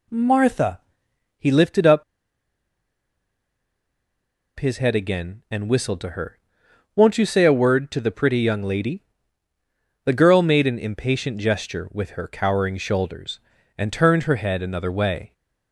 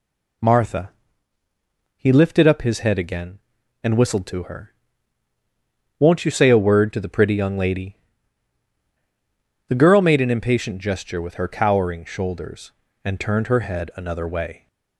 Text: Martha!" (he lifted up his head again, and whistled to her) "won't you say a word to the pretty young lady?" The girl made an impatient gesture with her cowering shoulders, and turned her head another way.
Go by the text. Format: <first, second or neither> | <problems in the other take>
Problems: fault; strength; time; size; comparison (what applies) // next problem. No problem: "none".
second | pauses between "up" and "his"; strong; at 2.0 s; 2.5 s long